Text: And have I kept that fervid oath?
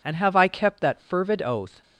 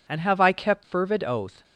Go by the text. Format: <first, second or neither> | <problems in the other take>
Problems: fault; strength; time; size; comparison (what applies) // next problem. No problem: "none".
first | skips "that"; at 0.8 s